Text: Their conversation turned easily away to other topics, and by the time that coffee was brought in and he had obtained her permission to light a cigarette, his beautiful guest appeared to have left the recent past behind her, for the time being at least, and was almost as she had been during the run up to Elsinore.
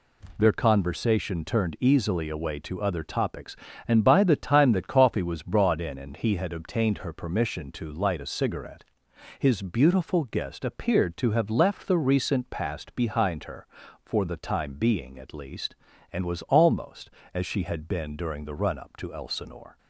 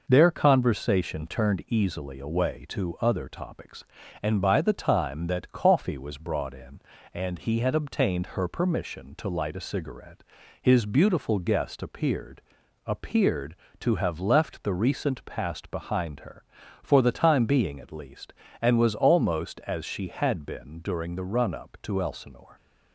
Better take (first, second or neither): first